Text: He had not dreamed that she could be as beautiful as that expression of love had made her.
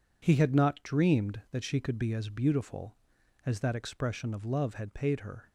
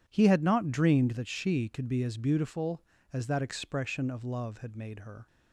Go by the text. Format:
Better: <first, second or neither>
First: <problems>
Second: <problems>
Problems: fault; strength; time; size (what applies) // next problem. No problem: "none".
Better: second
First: says "paid" for "made"; at 4.9 s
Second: none